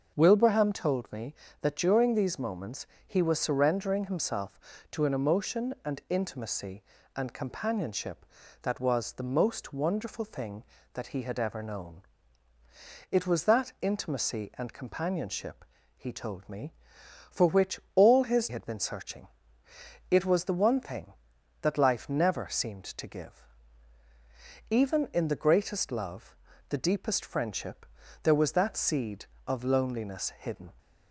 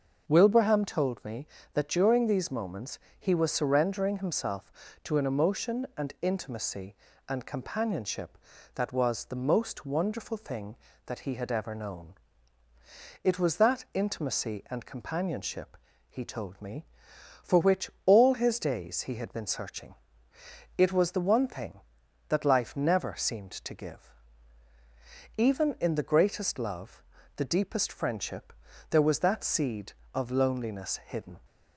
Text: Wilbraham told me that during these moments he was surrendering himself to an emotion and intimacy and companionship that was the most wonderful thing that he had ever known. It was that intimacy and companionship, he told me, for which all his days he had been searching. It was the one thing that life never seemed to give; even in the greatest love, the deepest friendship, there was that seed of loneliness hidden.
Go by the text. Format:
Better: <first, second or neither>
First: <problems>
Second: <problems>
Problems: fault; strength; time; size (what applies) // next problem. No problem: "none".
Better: second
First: starts louder than the rest; until 1.1 s; 6.5 dB // pauses between "moments" and "he"; slight; at 2.8 s; 0.20 s long // skips "days he"; at 18.4 s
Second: starts louder than the rest; until 1.2 s; 6.5 dB // pauses between "moments" and "he"; slight; at 2.9 s; 0.20 s long